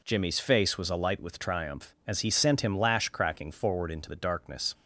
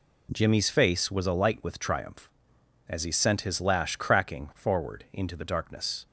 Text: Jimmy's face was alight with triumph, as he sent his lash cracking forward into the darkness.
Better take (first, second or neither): second